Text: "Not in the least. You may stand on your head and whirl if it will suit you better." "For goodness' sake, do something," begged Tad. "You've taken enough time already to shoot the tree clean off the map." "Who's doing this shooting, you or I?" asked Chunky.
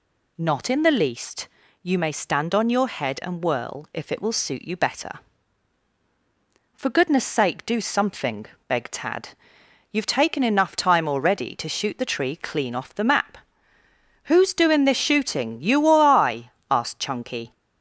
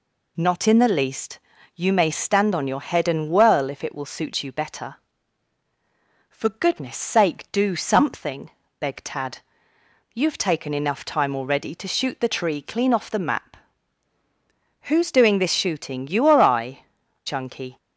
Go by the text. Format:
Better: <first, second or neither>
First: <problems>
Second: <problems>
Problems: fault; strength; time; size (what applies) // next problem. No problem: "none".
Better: first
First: none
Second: skips "asked"; at 17.0 s